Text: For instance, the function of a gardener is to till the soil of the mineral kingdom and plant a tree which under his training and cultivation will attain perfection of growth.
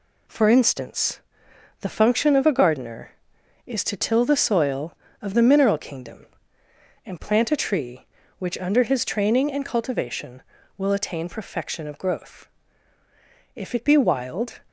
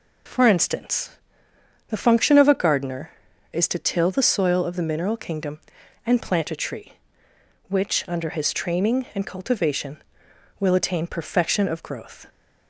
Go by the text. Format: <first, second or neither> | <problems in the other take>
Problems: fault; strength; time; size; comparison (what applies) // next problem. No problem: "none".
second | goes on to say "If it be wild"; noticeable; from 13.5 s on; 1.0 s long